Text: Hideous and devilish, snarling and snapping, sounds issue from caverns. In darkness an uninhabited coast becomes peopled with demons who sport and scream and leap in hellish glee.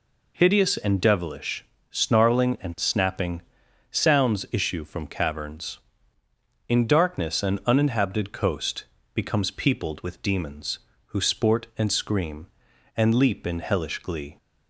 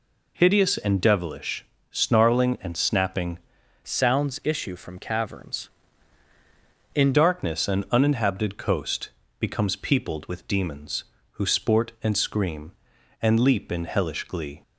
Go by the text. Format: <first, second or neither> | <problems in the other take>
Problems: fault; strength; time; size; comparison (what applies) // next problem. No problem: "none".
first | changes voice from "sounds" to "In"; from 3.8 to 7.1 s; 3.3 s long // pauses between "coast" and "becomes"; slight; at 9.1 s; 0.30 s long; slight in the first